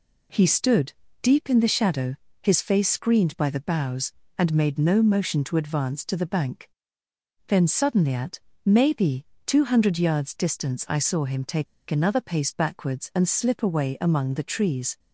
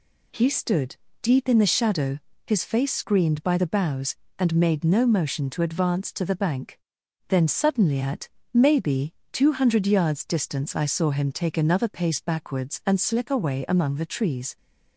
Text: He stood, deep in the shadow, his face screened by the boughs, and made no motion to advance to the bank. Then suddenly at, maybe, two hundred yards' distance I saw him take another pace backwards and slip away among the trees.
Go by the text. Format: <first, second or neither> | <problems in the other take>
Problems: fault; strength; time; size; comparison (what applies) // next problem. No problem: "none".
second | pauses between "take" and "another"; slight; at 11.6 s; 0.24 s long